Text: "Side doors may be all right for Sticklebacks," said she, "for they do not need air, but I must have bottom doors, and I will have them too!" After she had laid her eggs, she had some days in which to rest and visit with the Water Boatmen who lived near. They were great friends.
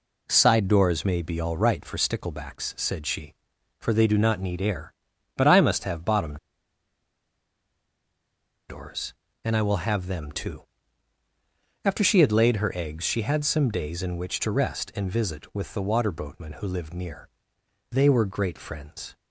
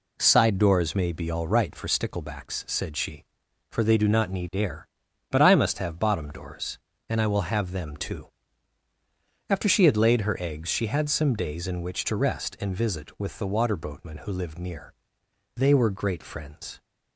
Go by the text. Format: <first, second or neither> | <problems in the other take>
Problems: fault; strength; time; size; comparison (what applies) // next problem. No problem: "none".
second | pauses between "bottom" and "doors"; strong; at 6.3 s; 2.3 s long